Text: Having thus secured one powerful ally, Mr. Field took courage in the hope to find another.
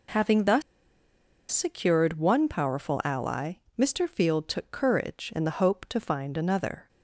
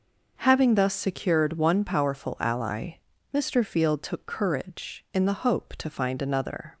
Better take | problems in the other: second | pauses between "thus" and "secured"; noticeable; at 0.6 s; 0.89 s long

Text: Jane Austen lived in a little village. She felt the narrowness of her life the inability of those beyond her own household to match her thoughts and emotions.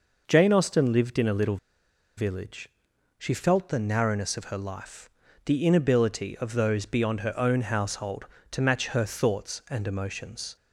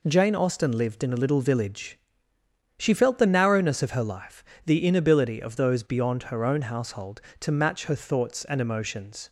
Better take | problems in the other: second | pauses between "little" and "village"; noticeable; at 1.5 s; 0.59 s long // pauses between "life" and "the"; slight; at 5.0 s; 0.36 s long; slight in the second

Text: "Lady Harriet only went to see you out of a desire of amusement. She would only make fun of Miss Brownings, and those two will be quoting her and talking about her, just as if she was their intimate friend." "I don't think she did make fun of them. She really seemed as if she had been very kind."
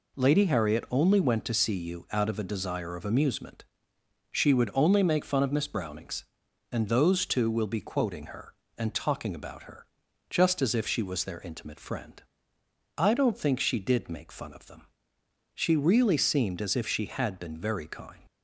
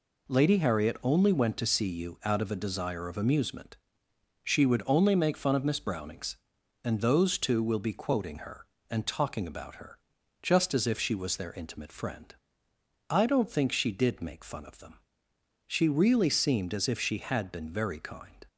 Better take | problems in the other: second | leaves "kind" unfinished; at 18.2 s; 75 ms

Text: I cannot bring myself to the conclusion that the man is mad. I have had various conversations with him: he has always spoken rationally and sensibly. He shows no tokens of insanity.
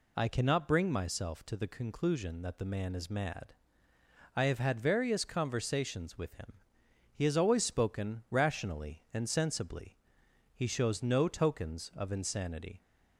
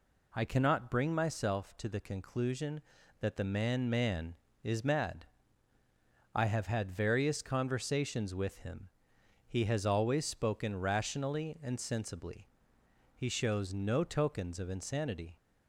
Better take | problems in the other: first | says "man" twice; at 3.8 s

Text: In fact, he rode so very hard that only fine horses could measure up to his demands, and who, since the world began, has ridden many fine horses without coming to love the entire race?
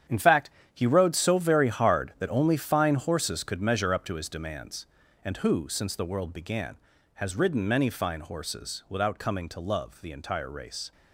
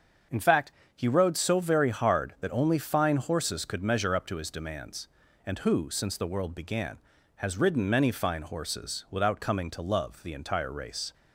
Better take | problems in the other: second | gets quieter; strong; throughout; 11 dB // starts louder than the rest; strong; until 1.3 s; 9.5 dB; also in the second

